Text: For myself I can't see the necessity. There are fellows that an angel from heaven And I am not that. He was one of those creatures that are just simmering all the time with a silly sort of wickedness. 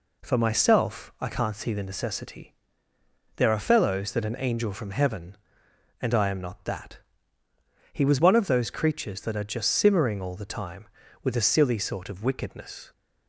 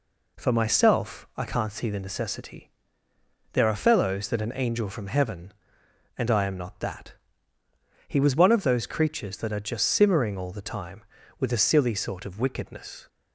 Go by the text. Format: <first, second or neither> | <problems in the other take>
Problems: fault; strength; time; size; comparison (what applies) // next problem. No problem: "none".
neither | none